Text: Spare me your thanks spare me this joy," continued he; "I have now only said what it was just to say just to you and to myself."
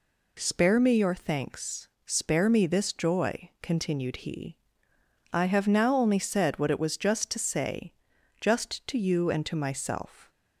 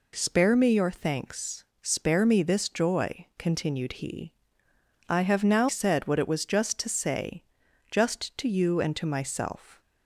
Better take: first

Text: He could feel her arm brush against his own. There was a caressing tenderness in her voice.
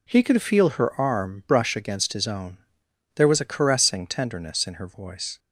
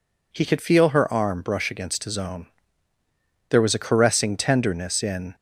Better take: first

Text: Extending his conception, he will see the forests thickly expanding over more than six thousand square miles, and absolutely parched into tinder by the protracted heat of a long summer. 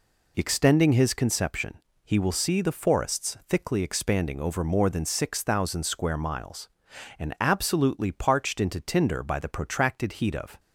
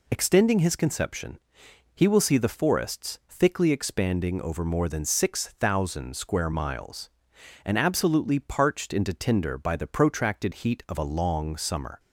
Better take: second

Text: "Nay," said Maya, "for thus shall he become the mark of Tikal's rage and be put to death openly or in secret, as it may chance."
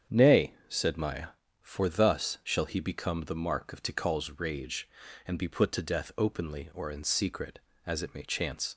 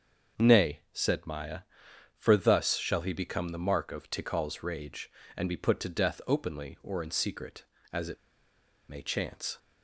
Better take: first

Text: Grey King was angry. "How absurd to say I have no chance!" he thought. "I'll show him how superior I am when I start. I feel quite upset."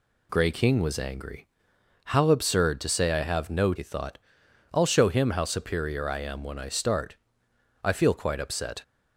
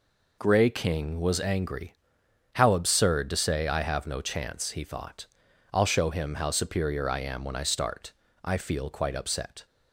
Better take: second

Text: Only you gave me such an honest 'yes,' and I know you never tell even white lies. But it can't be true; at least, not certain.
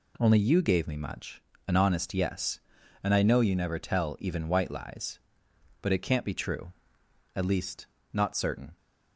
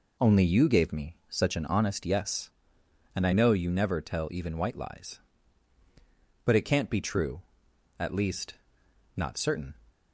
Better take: second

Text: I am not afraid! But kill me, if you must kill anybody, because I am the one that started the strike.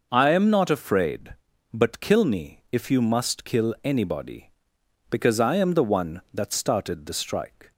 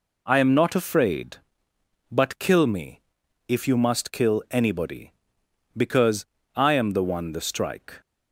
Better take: first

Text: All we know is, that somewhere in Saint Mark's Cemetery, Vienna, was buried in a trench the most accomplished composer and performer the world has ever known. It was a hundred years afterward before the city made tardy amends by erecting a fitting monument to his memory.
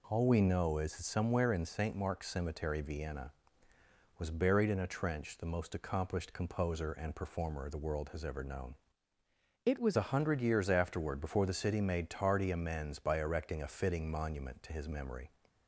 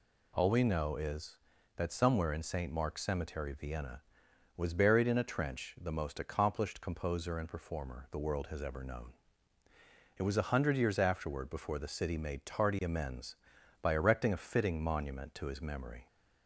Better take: second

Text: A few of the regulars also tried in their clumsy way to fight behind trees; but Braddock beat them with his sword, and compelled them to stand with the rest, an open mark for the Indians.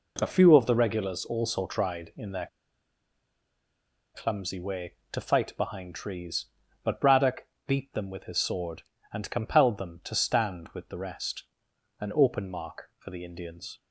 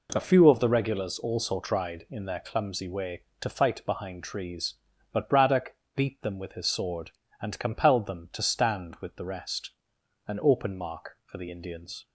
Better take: second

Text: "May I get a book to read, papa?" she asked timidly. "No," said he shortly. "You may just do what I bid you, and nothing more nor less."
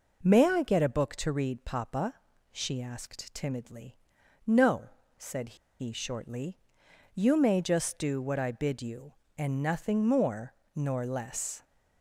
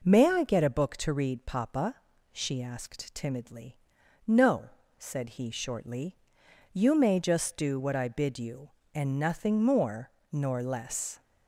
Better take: second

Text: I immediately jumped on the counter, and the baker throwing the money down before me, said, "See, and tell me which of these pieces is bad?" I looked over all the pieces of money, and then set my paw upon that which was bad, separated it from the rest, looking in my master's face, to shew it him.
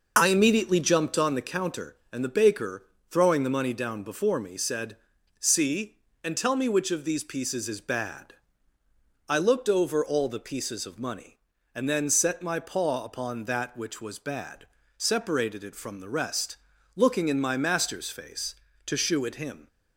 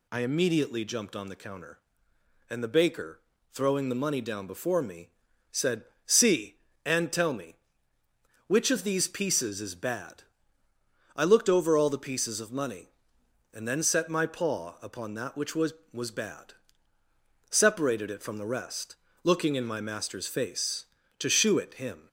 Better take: first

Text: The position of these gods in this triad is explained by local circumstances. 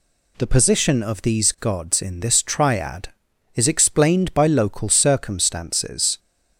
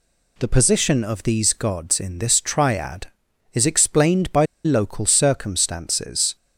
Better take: first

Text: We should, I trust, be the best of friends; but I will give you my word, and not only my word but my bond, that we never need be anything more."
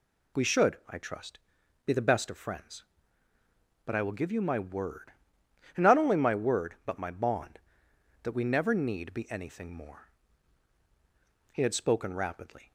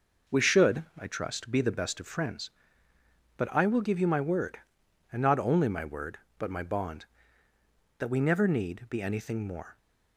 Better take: second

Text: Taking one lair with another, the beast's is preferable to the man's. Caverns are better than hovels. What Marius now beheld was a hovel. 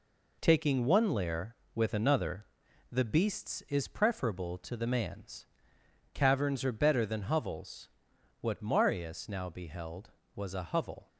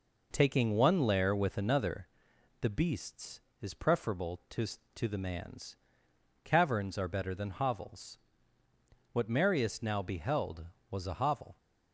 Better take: first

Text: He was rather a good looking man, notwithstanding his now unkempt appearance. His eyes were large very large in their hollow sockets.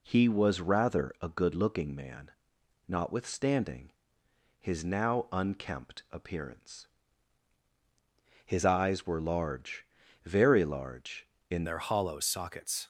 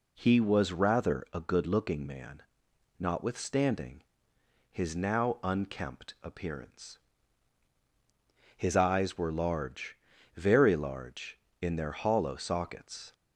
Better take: second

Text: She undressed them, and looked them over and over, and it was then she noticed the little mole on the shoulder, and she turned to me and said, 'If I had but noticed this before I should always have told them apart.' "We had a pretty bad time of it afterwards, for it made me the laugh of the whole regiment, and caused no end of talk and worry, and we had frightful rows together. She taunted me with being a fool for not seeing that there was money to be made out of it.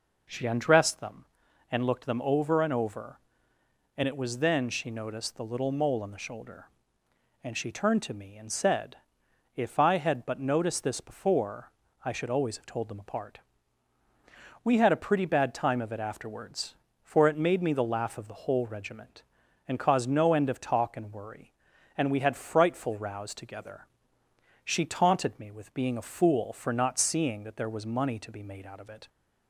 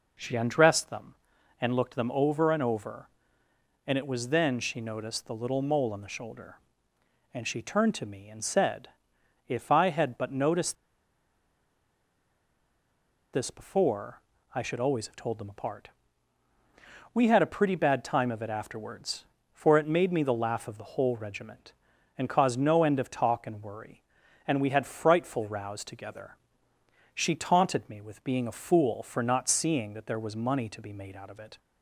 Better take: first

